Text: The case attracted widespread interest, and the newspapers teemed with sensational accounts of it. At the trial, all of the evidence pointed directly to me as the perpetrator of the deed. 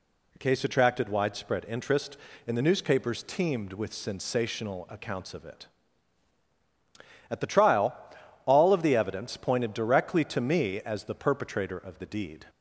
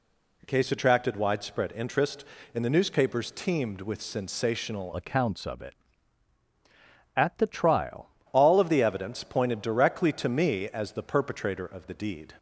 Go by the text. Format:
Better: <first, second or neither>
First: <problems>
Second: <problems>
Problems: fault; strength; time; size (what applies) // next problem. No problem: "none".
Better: first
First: none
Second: changes voice from "accounts" to "trial"; from 4.9 to 8.0 s; 3.1 s long